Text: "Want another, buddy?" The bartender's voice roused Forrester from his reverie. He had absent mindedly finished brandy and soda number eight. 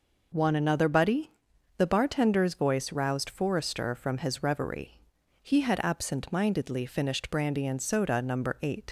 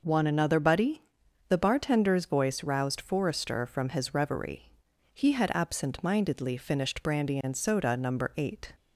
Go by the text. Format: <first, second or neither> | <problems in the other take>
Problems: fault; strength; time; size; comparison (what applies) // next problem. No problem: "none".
second | leaves "eight" unfinished; at 8.8 s; 90 ms